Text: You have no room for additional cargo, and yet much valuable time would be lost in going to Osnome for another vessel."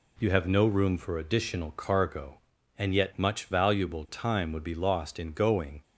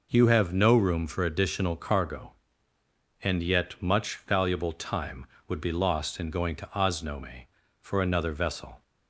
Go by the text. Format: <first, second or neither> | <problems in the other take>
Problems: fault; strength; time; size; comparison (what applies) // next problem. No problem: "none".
second | stops before "to Osnome for another vessel"; at 5.8 s